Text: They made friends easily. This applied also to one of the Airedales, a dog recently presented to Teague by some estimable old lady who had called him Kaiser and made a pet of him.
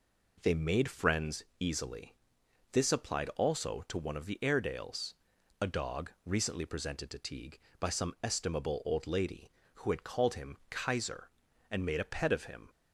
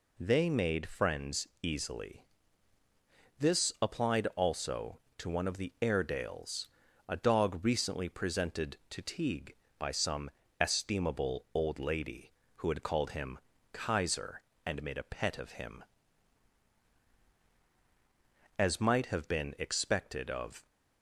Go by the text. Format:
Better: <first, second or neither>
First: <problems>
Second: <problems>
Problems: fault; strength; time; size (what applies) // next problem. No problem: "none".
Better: first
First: pauses between "friends" and "easily"; slight; at 1.4 s; 0.16 s long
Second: pauses between "friends" and "easily"; slight; at 1.4 s; 0.16 s long // pauses between "some" and "estimable"; slight; at 10.2 s; 0.30 s long // pauses between "him" and "Kaiser"; slight; at 13.3 s; 0.36 s long // goes on to say "As might have been expected of"; strong; from 18.5 s on; 2.0 s long